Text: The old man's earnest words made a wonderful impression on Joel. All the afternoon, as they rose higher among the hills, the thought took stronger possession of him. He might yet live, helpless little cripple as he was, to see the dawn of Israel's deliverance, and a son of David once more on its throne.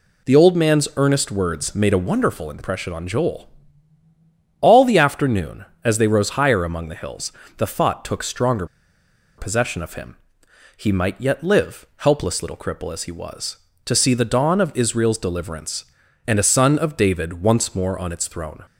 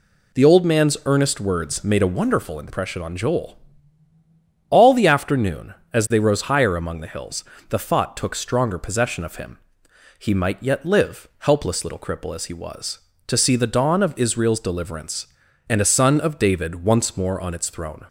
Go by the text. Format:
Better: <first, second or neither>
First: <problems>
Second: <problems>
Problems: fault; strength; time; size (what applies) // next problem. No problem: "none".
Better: second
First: pauses between "stronger" and "possession"; noticeable; at 8.6 s; 0.72 s long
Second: none